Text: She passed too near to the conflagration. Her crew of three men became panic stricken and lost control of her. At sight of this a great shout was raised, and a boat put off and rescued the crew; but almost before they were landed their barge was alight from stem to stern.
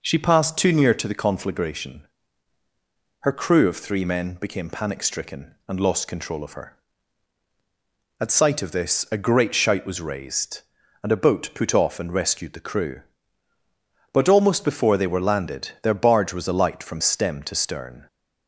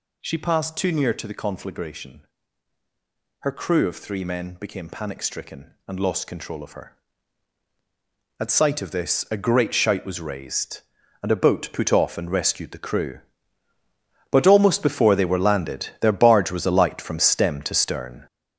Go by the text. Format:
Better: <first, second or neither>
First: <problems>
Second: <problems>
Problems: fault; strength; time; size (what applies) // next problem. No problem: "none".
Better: first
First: none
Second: gets louder; strong; throughout; 7.5 dB